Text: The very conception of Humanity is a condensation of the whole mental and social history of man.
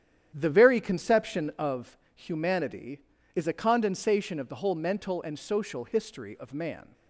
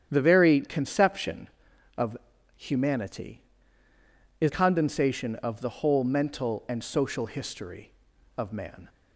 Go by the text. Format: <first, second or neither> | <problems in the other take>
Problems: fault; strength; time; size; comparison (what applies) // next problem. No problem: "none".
first | starts louder than the rest; strong; until 1.1 s; 9 dB; strong in the first // pauses between "of" and "Humanity"; at 2.1 s; 0.44 s long; slight in the first // skips "a"; at 4.4 s